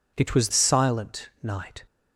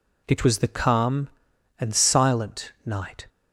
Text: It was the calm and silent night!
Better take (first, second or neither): second